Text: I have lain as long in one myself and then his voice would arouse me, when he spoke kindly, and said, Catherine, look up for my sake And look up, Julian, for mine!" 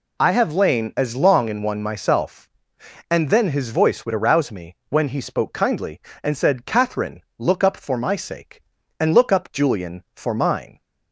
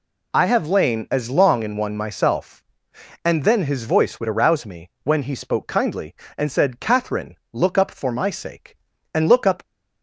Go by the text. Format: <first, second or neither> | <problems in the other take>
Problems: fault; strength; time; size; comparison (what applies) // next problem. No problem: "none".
first | stops before "Julian for mine"; at 9.6 s